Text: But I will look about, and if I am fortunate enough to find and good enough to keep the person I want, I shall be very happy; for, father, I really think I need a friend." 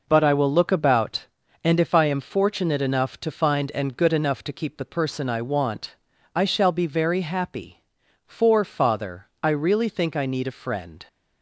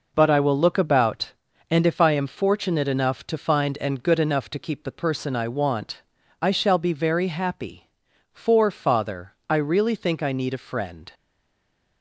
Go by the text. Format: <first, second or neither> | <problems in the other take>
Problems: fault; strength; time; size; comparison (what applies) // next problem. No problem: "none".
first | stays silent after the last word; slight; from 11.1 s on; 0.9 s long